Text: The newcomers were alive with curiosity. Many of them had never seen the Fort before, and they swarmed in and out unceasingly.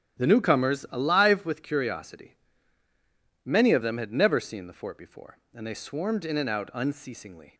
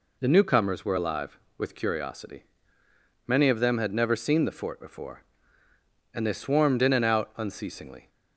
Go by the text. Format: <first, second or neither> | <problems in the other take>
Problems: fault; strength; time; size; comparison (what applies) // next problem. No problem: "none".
second | starts louder than the rest; strong; until 1.2 s; 12 dB // skips "were"; at 0.8 s